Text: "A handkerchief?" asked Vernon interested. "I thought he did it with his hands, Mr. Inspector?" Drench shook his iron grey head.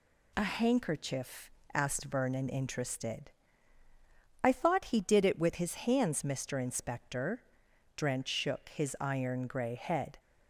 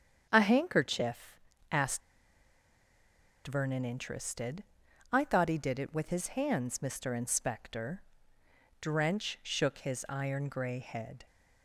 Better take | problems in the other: first | starts louder than the rest; strong; until 1.3 s; 8 dB // pauses between "asked" and "Vernon"; strong; at 2.0 s; 1.4 s long

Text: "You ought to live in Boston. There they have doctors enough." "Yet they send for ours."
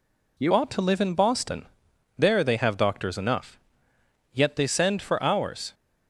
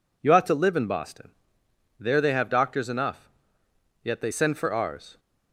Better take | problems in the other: second | changes voice at "ought"; from 0.5 s on; 5.2 s long

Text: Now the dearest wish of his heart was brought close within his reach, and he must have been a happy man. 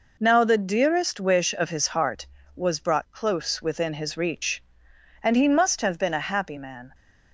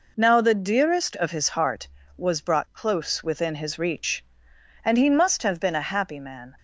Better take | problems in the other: first | skips "wish"; at 1.1 s

